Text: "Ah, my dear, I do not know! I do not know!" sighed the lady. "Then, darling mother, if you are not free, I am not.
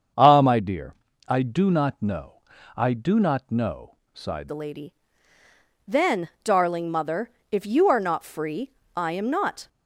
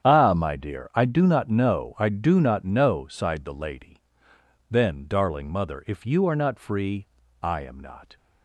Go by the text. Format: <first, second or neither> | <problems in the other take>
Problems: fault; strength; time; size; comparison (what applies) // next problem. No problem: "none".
second | starts louder than the rest; strong; until 1.5 s; 7.5 dB; strong in the second // changes voice at "the"; from 4.4 s on; 5.2 s long